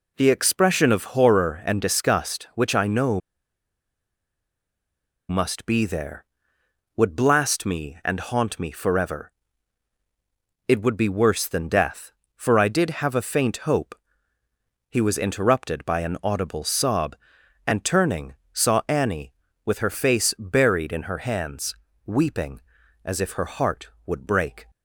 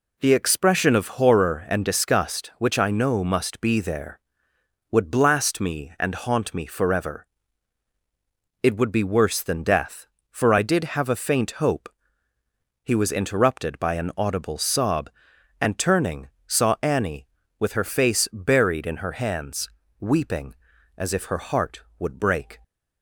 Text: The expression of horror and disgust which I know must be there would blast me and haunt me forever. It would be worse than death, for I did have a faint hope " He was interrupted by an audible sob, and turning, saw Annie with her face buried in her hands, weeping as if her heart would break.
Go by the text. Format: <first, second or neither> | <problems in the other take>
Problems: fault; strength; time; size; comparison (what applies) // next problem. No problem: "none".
second | pauses between "know" and "must"; strong; at 3.2 s; 2.0 s long